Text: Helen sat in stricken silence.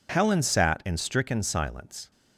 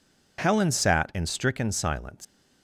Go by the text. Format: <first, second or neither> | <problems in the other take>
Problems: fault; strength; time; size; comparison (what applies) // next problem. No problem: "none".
first | leaves "silence" unfinished; at 2.2 s; 145 ms